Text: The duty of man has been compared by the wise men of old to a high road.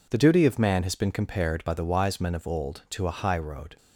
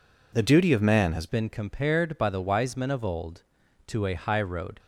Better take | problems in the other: first | changes voice at "been"; from 1.2 s on; 3.5 s long

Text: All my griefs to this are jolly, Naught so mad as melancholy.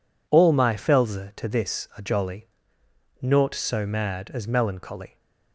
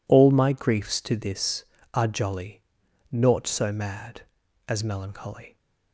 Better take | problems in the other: second | says "felze" for "griefs"; at 0.7 s

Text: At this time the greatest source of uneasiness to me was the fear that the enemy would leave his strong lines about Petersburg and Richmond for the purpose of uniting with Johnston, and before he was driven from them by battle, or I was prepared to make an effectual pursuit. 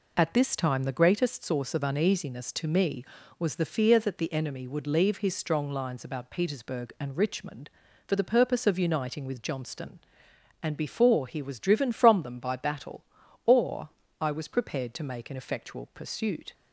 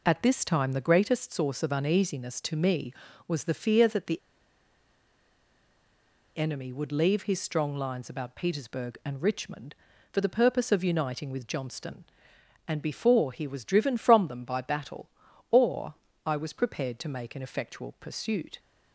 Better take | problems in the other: first | pauses between "the" and "enemy"; strong; at 4.1 s; 2.1 s long // pauses between "or" and "I"; slight; at 15.9 s; 0.30 s long; slight in the first

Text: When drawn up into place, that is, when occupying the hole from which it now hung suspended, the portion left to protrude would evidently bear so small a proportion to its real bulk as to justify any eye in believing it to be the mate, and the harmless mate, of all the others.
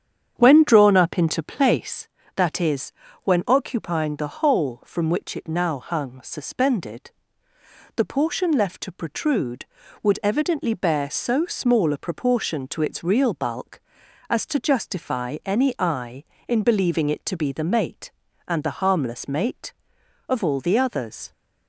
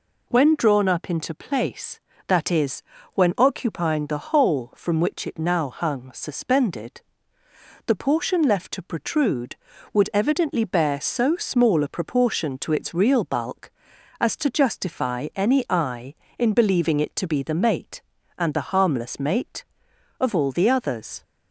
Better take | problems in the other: second | starts louder than the rest; strong; until 2.1 s; 8.5 dB

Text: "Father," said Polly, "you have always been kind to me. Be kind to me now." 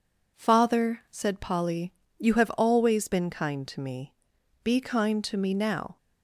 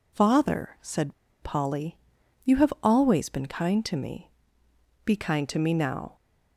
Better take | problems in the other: first | pauses between "said" and "Polly"; slight; at 1.1 s; 0.29 s long

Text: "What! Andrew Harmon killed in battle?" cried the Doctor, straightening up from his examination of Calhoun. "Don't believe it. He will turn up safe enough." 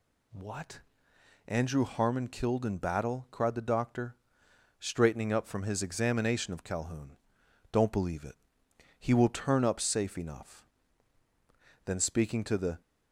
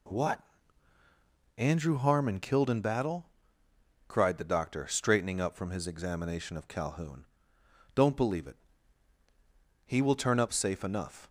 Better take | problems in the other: second | goes on to say "Then speaking to the"; noticeable; from 11.8 s on; 0.96 s long

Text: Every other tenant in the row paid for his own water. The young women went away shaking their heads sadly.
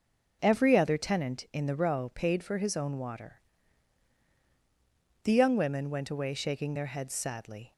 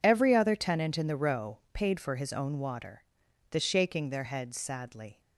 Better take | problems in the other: first | pauses between "row" and "paid"; slight; at 1.5 s; 0.16 s long // skips "young women went away"; at 3.5 s

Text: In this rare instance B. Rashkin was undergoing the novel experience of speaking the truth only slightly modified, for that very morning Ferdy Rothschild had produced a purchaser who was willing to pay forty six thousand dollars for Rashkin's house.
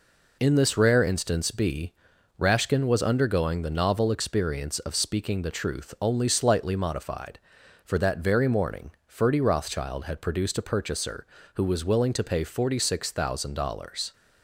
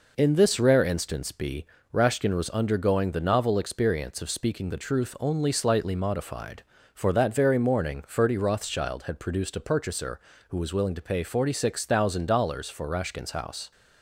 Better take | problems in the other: second | pauses between "morning" and "Ferdy"; slight; at 8.9 s; 0.16 s long // stops before "for Rashkin's house"; at 14.1 s

